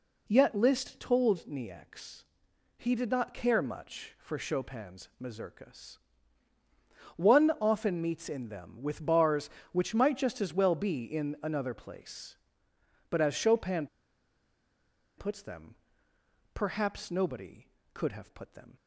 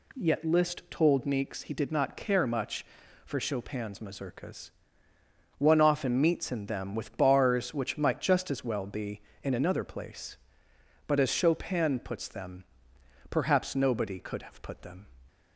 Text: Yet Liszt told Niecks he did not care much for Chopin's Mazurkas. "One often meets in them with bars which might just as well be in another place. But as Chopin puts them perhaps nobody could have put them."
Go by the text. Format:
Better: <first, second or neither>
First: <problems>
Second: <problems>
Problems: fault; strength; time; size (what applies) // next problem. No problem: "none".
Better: second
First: pauses between "Niecks" and "he"; noticeable; at 2.2 s; 0.52 s long // pauses between "Chopin" and "puts"; strong; at 13.8 s; 1.3 s long // pauses between "them" and "perhaps"; noticeable; at 15.7 s; 0.78 s long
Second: pauses between "them" and "perhaps"; noticeable; at 12.6 s; 0.66 s long